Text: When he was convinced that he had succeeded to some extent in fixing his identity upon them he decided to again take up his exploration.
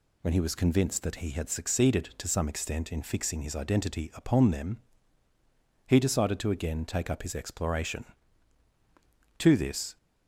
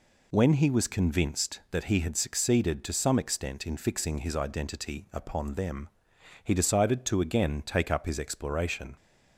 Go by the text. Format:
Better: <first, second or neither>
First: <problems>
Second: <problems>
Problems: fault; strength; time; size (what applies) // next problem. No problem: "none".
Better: second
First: pauses between "them" and "he"; at 4.8 s; 1.0 s long // goes on to say "To this"; from 9.3 s on; 0.58 s long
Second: pauses between "them" and "he"; noticeable; at 5.8 s; 0.56 s long